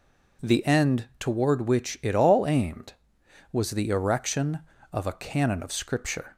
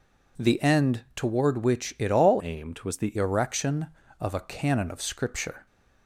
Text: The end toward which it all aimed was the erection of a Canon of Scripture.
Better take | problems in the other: first | changes voice from "aimed" to "the"; from 2.4 to 3.1 s; 0.7 s long

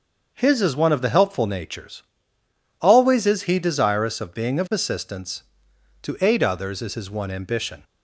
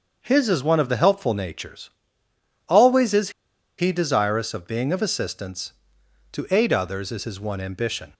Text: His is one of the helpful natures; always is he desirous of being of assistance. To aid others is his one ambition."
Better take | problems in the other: first | starts louder than the rest; until 1.2 s; 6.5 dB; also in the first // pauses between "is" and "he"; noticeable; at 3.2 s; 0.48 s long

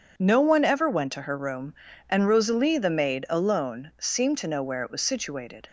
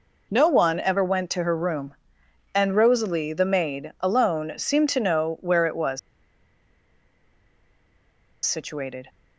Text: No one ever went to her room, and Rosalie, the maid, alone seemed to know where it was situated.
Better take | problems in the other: first | pauses between "was" and "situated"; strong; at 5.9 s; 2.4 s long

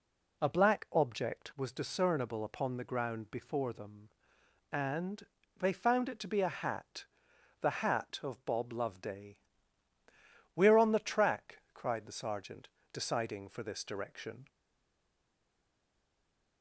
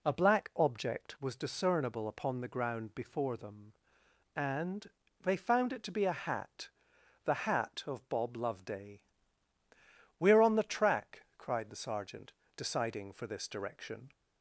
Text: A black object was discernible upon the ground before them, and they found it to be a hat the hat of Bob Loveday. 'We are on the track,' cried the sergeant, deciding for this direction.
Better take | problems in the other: second | pauses between "and" and "they"; slight; at 5.2 s; 0.36 s long; slight in the second // pauses between "hat" and "the"; noticeable; at 7.0 s; 0.56 s long; noticeable in the second // stays silent after the last word; from 14.4 s on; 2.2 s long

